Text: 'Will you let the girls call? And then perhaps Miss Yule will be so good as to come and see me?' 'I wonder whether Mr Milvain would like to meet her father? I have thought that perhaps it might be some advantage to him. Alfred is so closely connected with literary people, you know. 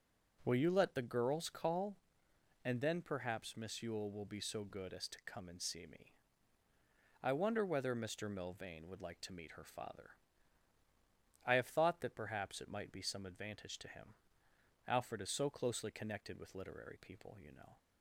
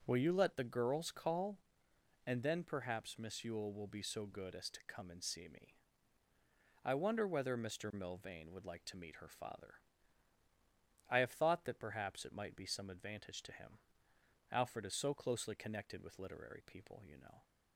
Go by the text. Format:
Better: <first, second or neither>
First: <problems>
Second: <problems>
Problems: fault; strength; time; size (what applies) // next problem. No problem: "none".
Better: neither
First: none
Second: none